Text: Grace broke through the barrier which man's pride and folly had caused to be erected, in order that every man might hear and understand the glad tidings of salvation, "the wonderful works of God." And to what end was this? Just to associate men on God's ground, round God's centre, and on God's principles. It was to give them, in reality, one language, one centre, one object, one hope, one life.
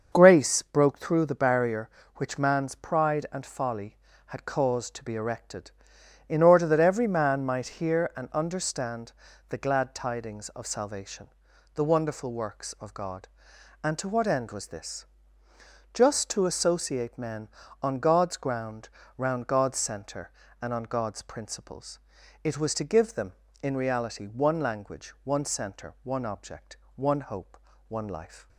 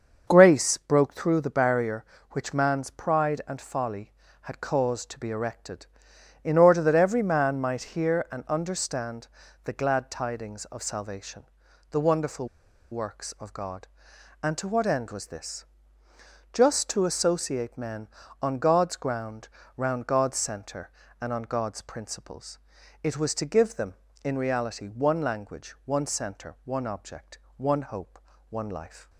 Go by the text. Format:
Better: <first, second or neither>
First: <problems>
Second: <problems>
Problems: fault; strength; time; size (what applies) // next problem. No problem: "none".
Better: first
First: starts louder than the rest; until 1.1 s; 6.5 dB // pauses between "understand" and "the"; at 9.1 s; 0.38 s long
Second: starts louder than the rest; until 1.2 s; 6.5 dB // pauses between "understand" and "the"; at 9.2 s; 0.38 s long // pauses between "wonderful" and "works"; at 12.4 s; 0.45 s long